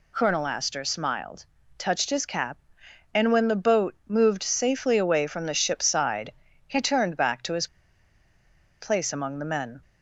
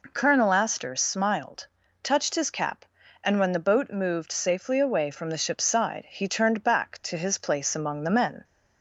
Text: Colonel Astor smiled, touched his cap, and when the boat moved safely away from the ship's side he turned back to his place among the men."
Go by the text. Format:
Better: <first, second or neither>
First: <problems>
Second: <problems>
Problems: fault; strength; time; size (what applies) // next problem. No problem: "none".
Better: second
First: pauses between "side" and "he"; slight; at 6.3 s; 0.36 s long // pauses between "his" and "place"; at 7.6 s; 1.1 s long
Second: none